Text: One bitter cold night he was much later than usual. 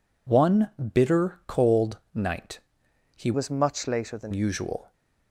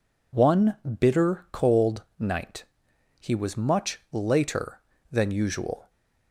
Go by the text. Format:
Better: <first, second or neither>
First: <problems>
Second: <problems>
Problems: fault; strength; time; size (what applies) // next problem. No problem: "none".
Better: second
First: pauses between "One" and "bitter"; slight; at 0.7 s; 0.20 s long // pauses between "night" and "he"; noticeable; at 2.5 s; 0.56 s long // changes voice from "was" to "than"; from 3.3 to 4.3 s; 1.0 s long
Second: pauses between "One" and "bitter"; slight; at 0.7 s; 0.20 s long // pauses between "night" and "he"; noticeable; at 2.6 s; 0.55 s long